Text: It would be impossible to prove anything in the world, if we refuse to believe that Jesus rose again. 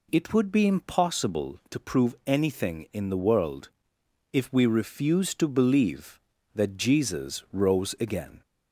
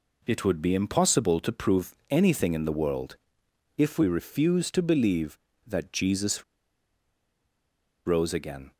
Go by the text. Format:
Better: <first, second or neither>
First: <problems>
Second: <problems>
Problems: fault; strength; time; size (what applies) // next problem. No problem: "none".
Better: first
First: none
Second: pauses between "Jesus" and "rose"; strong; at 6.4 s; 1.6 s long